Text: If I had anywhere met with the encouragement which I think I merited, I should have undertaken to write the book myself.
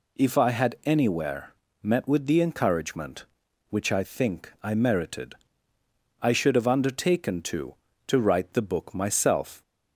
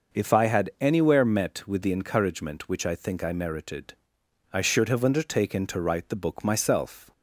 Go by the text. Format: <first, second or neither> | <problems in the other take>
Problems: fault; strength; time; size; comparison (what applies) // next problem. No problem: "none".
second | pauses between "anywhere" and "met"; slight; at 1.5 s; 0.28 s long // says "to" twice; at 8.0 s